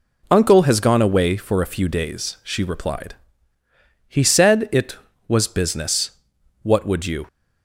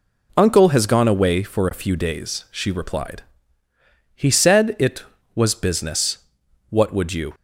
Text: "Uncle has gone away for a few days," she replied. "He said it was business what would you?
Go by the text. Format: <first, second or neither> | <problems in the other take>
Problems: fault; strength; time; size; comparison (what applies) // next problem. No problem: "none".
neither | pauses between "business" and "what"; noticeable; the same in both